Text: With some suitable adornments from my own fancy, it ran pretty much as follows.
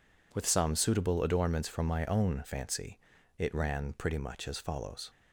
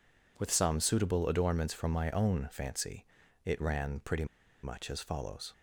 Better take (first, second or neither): first